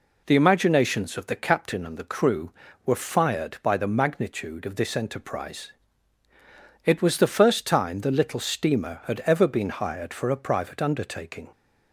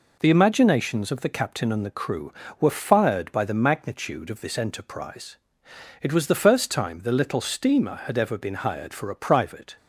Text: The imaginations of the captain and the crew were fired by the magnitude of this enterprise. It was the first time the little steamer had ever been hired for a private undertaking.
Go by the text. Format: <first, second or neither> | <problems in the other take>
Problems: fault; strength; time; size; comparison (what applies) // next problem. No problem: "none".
first | stops before "undertaking"; at 9.7 s